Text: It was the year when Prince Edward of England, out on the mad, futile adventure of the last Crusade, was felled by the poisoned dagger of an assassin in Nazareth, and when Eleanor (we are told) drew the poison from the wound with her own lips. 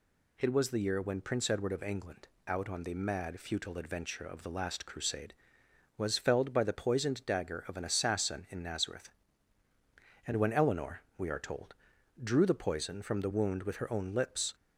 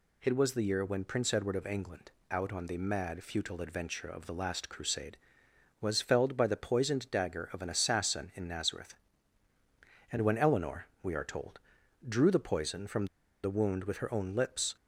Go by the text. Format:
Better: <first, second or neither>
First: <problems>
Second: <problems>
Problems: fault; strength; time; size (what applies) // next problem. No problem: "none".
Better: first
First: none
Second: pauses between "from" and "the"; at 13.0 s; 0.37 s long